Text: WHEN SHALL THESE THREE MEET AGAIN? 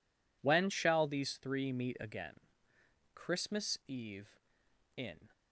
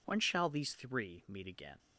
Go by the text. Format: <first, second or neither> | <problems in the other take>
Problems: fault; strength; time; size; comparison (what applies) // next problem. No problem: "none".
second | goes on to say "Christmas Eve in"; strong; from 3.1 s on; 2.1 s long